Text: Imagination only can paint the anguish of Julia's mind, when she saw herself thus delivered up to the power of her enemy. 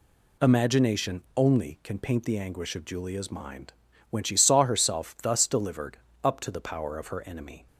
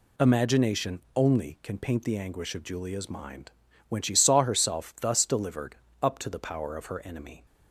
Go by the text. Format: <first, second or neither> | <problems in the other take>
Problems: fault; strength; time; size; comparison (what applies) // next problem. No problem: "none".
neither | pauses between "delivered" and "up"; slight; the same in both